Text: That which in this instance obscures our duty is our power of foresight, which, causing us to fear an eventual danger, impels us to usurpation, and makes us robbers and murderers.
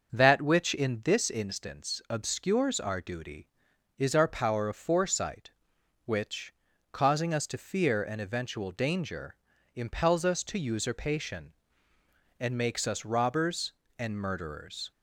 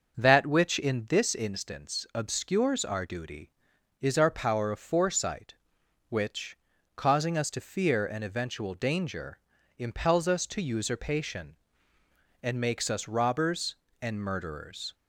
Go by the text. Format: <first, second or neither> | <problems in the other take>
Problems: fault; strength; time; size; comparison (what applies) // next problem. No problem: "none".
neither | starts louder than the rest; the same in both